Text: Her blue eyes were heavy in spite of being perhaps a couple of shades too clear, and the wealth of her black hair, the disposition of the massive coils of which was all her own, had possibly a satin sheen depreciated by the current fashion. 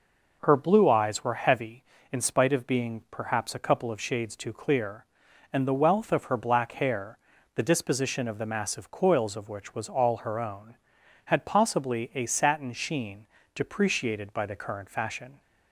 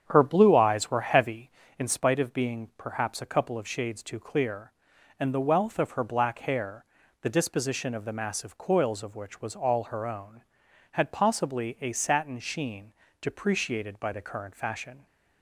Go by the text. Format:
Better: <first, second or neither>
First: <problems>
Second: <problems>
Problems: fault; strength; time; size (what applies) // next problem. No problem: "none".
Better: first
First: pauses between "sheen" and "depreciated"; slight; at 13.2 s; 0.28 s long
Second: starts louder than the rest; strong; until 2.0 s; 8.5 dB // pauses between "sheen" and "depreciated"; slight; at 12.9 s; 0.28 s long